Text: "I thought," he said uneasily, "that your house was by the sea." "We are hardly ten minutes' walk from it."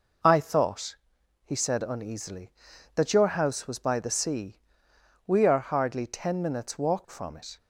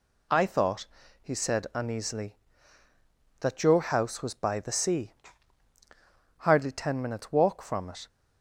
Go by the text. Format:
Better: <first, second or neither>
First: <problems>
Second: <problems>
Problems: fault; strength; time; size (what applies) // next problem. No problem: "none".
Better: first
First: none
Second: skips "We are"; at 5.7 s